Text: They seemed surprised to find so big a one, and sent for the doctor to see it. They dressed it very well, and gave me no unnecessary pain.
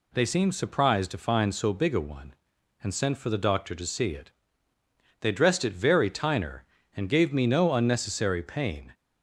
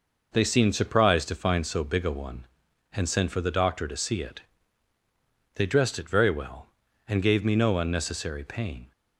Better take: second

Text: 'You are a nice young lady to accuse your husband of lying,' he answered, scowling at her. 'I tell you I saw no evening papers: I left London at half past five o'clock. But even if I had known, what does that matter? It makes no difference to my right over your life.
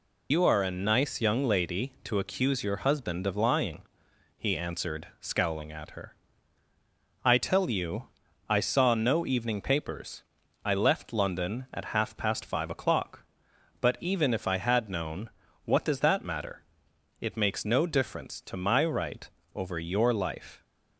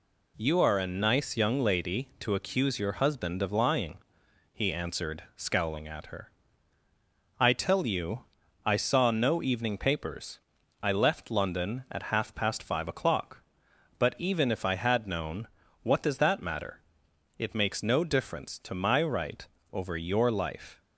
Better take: second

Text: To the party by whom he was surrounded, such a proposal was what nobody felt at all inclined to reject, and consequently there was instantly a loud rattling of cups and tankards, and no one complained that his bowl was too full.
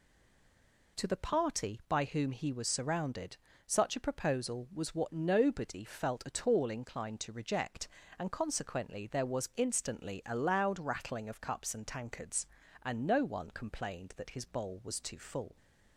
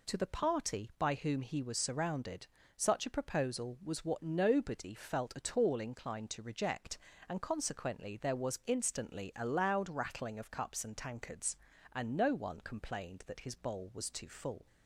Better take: second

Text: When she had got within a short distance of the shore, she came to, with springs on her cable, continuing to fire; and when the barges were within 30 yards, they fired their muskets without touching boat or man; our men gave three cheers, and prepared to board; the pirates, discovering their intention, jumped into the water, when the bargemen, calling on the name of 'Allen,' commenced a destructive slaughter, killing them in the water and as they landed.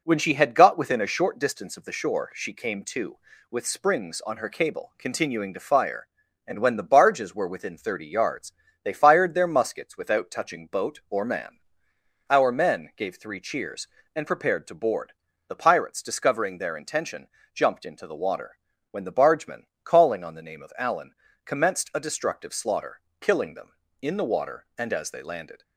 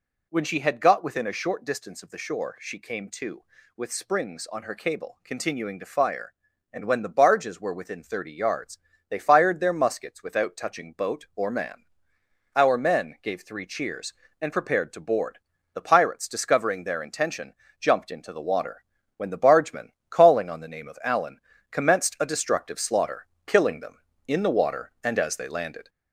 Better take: first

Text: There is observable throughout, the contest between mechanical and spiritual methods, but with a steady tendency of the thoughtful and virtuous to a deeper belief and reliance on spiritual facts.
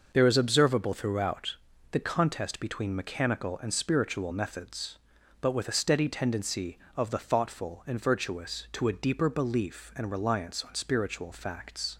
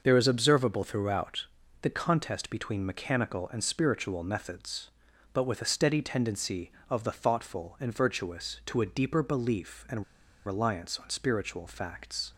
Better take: first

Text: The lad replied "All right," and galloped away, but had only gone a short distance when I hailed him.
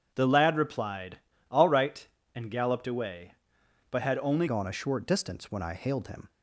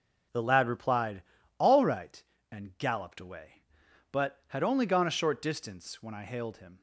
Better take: second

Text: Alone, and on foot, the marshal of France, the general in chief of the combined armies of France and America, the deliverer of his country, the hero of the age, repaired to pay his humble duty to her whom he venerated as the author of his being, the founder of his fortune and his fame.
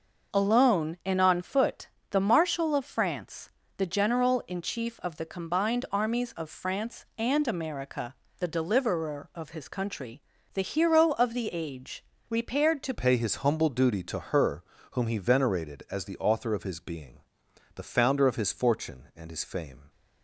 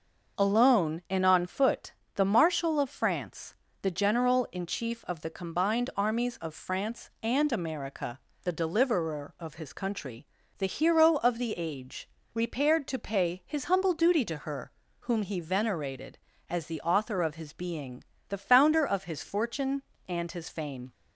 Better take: second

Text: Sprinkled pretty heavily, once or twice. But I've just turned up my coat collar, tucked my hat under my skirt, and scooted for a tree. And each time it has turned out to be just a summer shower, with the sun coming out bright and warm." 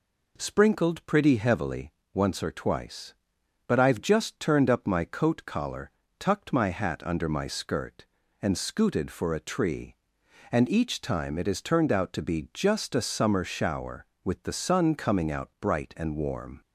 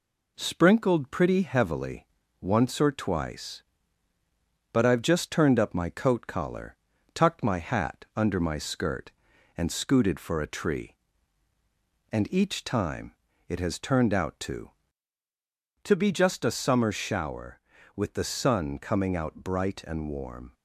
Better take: first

